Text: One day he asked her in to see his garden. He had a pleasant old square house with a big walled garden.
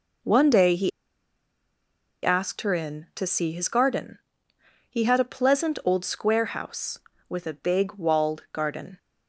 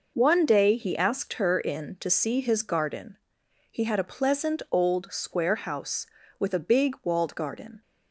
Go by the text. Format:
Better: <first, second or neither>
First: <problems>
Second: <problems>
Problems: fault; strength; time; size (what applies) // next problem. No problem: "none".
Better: second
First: pauses between "he" and "asked"; strong; at 0.9 s; 1.3 s long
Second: none